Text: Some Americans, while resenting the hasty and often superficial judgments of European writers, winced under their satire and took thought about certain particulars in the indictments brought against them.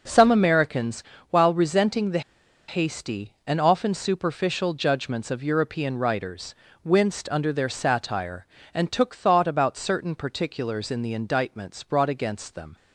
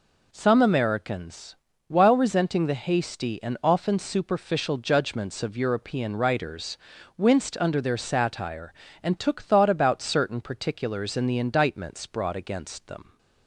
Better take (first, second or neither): second